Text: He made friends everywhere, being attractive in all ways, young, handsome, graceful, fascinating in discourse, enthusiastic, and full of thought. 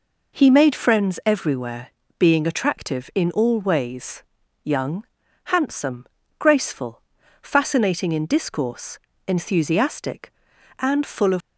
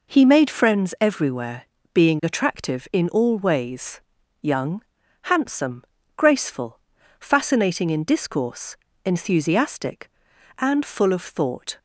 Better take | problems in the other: second | stops before "thought"; at 11.4 s

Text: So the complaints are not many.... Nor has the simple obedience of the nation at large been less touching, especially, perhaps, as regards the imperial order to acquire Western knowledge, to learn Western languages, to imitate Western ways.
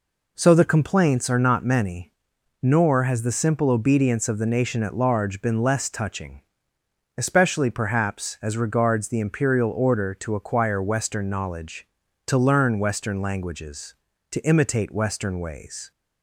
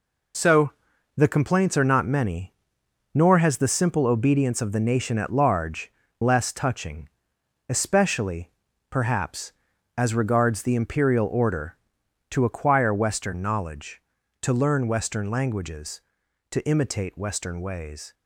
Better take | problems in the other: first | pauses between "So" and "the"; at 0.7 s; 0.44 s long // skips "been"; at 6.0 s

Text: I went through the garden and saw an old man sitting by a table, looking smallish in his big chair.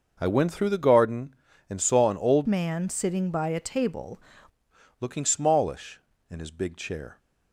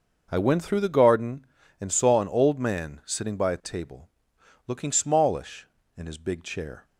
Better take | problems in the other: second | changes voice from "man" to "table"; from 2.4 to 4.1 s; 1.7 s long

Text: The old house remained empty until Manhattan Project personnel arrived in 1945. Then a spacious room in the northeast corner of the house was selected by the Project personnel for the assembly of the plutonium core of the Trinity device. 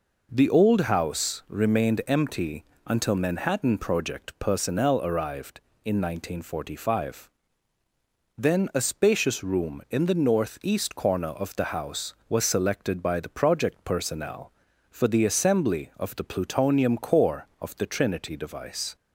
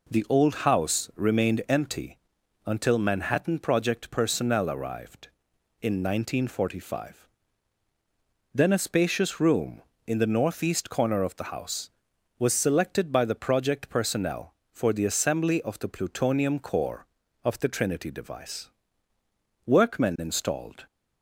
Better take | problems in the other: first | pauses between "empty" and "until"; noticeable; at 2.1 s; 0.48 s long; slight in the first // goes on to say "Workmen installed"; noticeable; from 19.6 s on; 1.2 s long

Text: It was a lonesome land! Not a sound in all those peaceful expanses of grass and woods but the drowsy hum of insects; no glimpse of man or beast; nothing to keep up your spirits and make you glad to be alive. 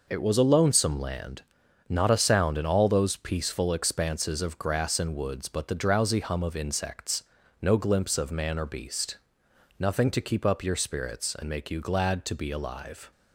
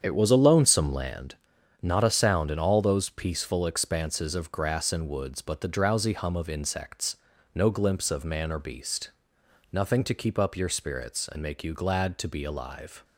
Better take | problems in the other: first | starts louder than the rest; strong; until 1.3 s; 8 dB

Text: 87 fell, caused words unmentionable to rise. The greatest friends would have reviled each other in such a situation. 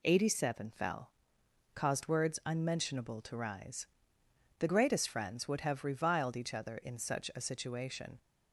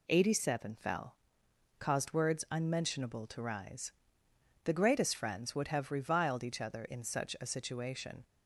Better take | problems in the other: neither | none

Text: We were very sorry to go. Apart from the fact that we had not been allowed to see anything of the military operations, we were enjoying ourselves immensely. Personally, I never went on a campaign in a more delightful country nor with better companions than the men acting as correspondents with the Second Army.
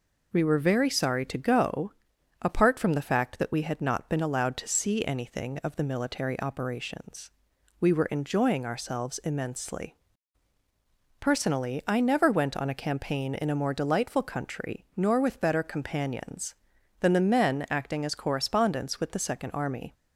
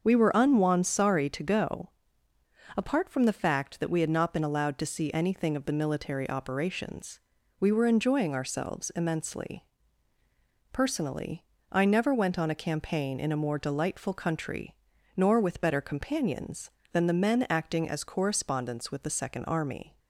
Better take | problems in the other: first | starts louder than the rest; until 1.0 s; 6.5 dB // says "unwon" for "very"; at 0.3 s // pauses between "country" and "nor"; noticeable; at 14.7 s; 0.46 s long

